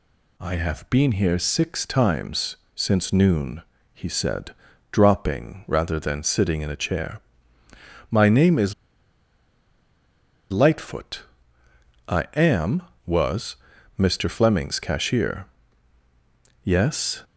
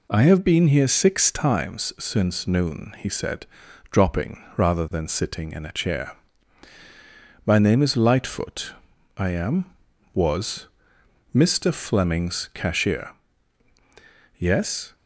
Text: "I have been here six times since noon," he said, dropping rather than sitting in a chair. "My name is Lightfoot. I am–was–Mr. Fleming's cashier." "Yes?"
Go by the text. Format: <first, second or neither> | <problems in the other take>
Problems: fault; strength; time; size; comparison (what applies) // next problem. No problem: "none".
second | pauses between "times" and "since"; slight; at 2.5 s; 0.18 s long // pauses between "is" and "Lightfoot"; strong; at 8.7 s; 1.7 s long